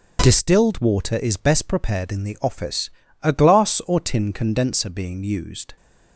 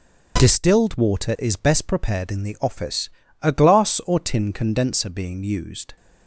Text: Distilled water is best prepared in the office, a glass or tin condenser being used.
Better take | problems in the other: neither | starts louder than the rest; the same in both

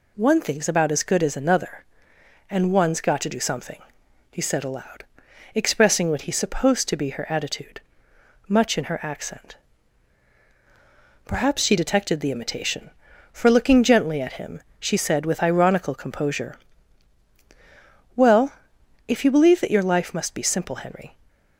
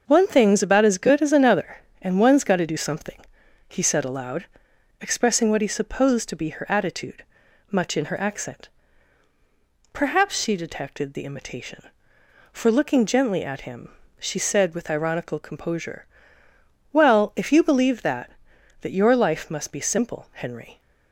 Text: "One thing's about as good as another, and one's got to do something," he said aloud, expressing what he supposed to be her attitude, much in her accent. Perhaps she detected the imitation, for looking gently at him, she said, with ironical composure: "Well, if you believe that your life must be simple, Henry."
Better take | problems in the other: first | starts louder than the rest; until 1.0 s; 6.5 dB // says "that" twice; at 18.8 s

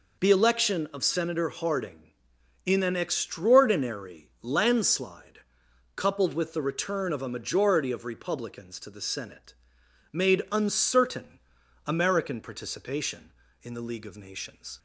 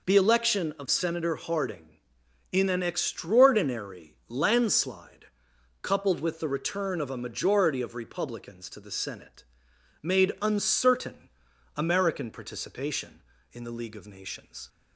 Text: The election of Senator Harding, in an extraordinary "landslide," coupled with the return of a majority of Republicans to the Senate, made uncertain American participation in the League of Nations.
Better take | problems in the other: neither | pauses between "uncertain" and "American"; the same in both

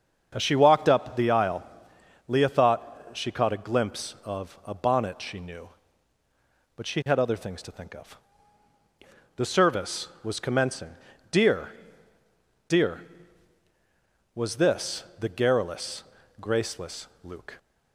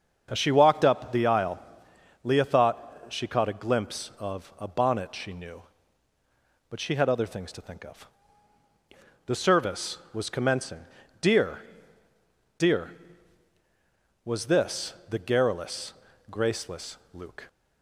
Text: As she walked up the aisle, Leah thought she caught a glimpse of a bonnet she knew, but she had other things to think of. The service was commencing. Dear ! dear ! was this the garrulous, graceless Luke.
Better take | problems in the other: neither | starts louder than the rest; the same in both // pauses between "this" and "the"; slight; the same in both // pauses between "graceless" and "Luke"; slight; the same in both

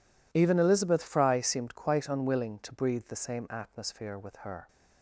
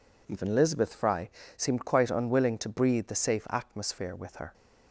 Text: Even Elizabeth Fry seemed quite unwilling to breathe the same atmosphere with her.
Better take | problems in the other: first | pauses between "Fry" and "seemed"; slight; at 1.2 s; 0.26 s long // says "safe" for "same"; at 3.1 s

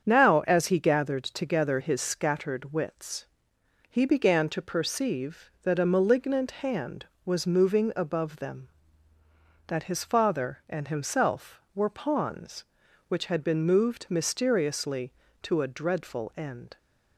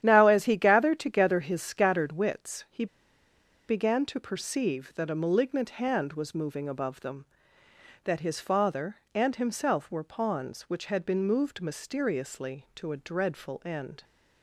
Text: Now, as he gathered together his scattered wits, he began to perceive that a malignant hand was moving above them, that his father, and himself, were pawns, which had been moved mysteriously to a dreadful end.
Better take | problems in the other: first | starts louder than the rest; strong; until 1.0 s; 10.5 dB; strong in the first // pauses between "he" and "began"; noticeable; at 2.8 s; 0.83 s long

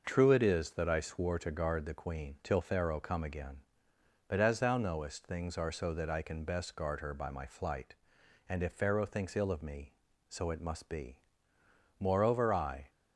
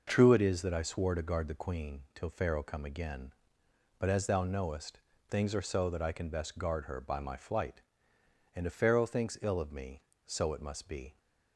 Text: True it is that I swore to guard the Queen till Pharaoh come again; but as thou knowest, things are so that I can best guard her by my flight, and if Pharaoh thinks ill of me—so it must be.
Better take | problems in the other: second | starts louder than the rest; noticeable; until 1.0 s; 6 dB // goes on to say "Moreover I"; noticeable; from 11.9 s on; 0.90 s long

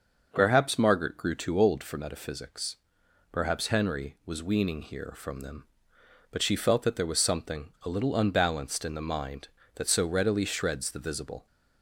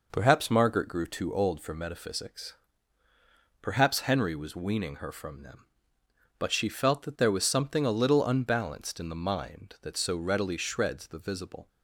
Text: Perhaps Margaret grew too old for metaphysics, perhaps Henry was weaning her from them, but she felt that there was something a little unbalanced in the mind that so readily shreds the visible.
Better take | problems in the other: second | says "here" for "her"; at 4.8 s

